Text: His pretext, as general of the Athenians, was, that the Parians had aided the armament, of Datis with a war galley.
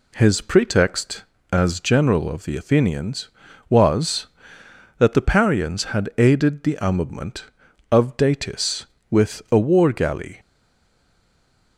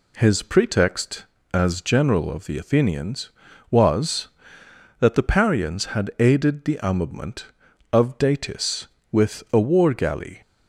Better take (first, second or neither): second